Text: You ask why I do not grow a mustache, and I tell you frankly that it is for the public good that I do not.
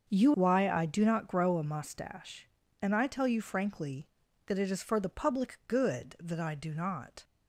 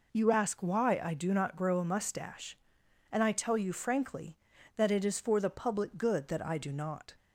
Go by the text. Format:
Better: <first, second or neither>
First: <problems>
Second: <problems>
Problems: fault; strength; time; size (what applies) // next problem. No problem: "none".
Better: second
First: starts louder than the rest; until 1.1 s; 6.5 dB // skips "ask"; at 0.3 s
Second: none